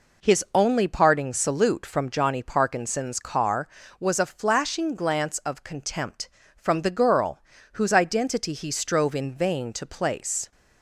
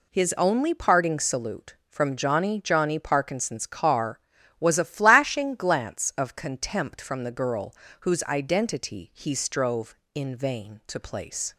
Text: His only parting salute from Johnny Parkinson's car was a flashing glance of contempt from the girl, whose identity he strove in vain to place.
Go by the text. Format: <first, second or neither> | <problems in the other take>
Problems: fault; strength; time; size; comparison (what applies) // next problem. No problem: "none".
first | says "Johnny" twice; at 2.6 s